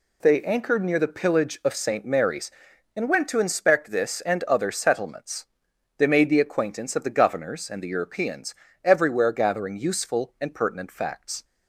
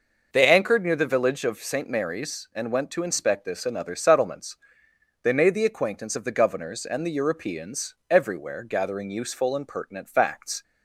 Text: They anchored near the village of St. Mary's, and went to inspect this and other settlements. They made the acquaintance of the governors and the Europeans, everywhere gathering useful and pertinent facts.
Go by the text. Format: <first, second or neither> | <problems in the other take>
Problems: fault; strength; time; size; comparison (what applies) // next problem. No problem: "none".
second | says "pillage" for "village"; at 1.0 s